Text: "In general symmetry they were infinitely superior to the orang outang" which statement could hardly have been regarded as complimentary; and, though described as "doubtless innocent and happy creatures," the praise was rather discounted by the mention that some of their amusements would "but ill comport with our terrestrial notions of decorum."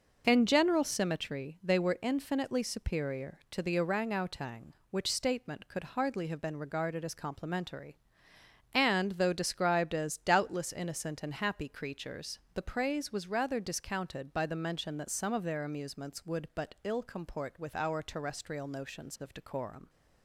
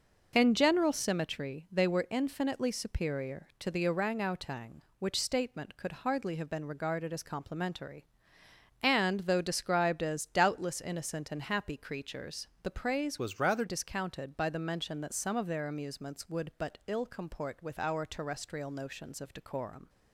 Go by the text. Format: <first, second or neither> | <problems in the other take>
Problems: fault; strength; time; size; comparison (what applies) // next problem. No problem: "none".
first | changes voice from "was" to "rather"; from 13.1 to 13.6 s; 0.5 s long